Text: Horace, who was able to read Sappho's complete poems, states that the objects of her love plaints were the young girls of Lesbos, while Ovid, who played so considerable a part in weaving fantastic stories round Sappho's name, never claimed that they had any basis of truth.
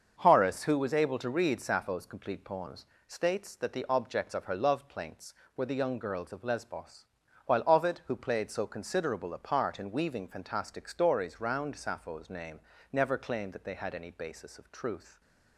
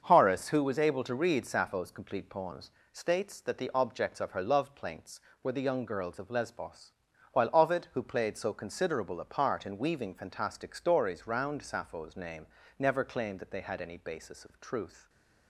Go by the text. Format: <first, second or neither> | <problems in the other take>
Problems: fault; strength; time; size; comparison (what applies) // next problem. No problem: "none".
neither | starts louder than the rest; the same in both